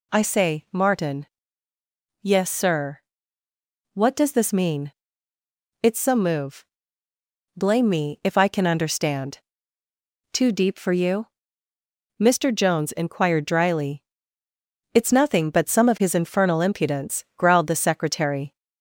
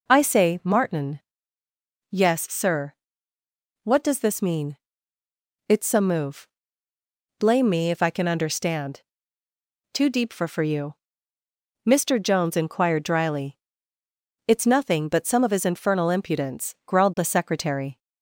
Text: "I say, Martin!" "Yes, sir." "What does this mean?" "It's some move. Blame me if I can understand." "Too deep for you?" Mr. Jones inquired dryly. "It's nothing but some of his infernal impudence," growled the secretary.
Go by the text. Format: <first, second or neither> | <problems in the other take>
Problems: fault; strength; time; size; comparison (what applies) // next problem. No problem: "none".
first | says "for" twice; at 10.4 s